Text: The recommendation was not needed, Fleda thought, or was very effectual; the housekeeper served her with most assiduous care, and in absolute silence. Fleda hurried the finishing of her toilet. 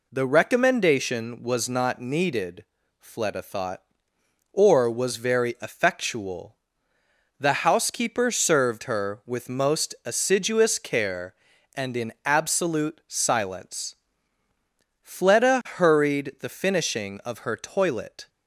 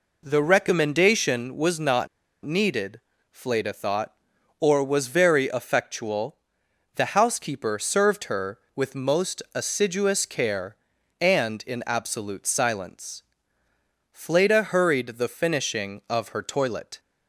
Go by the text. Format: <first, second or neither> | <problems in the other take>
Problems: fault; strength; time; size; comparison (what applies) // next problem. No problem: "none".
first | pauses between "not" and "needed"; slight; at 2.0 s; 0.35 s long